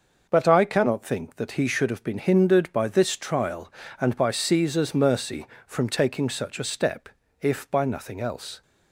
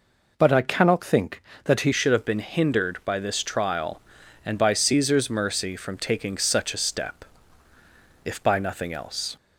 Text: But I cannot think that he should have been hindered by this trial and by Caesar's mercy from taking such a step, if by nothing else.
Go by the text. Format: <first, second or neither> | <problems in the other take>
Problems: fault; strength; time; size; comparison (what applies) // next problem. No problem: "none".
first | changes voice at "should"; from 1.9 s on; 7.4 s long